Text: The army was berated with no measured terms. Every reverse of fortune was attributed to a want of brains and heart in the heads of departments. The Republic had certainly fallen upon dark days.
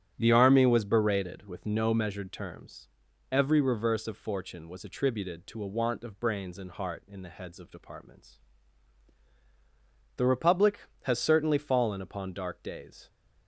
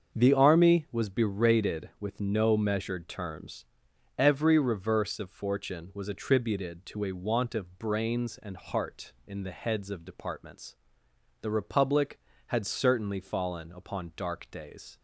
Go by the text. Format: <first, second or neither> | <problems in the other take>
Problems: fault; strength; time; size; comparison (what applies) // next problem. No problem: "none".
second | starts louder than the rest; strong; until 1.1 s; 9 dB; also in the second // says "has" for "had"; at 11.0 s